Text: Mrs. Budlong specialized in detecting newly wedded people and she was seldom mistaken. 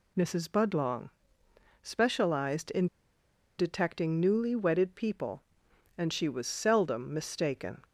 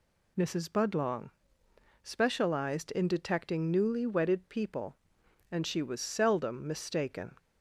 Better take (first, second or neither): second